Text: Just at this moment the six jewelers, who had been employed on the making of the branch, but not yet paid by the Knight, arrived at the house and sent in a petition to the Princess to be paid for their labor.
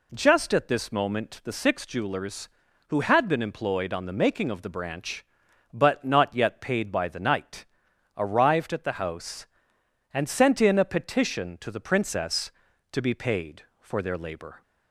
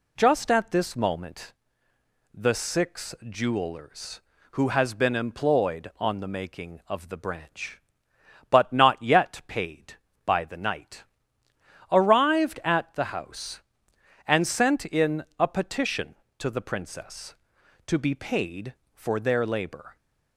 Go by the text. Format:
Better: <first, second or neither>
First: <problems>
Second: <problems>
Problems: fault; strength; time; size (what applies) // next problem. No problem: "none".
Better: first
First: none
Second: pauses between "moment" and "the"; noticeable; at 1.5 s; 0.80 s long // says "has" for "had"; at 4.6 s // pauses between "in" and "a"; slight; at 15.2 s; 0.16 s long